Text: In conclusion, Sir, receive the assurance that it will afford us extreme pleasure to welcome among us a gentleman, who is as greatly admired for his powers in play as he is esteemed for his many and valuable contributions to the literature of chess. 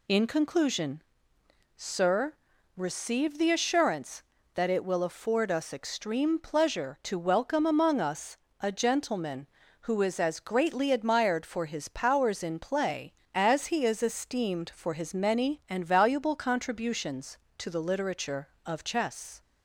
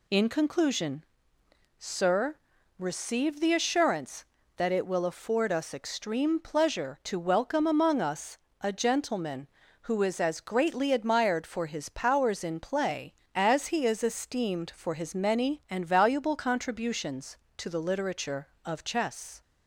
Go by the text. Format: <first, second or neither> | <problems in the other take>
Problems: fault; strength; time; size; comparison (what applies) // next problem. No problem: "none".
neither | pauses between "us" and "a"; slight; the same in both